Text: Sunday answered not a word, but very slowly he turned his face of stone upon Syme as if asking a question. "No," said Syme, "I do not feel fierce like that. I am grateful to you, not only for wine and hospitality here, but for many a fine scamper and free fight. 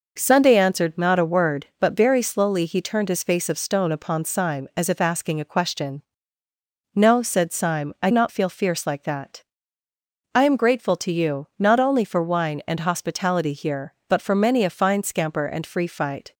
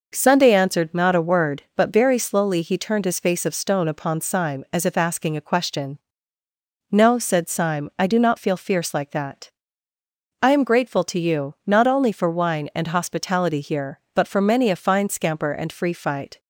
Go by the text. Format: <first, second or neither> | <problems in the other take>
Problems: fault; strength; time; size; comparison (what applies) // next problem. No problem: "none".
second | skips "do"; at 8.1 s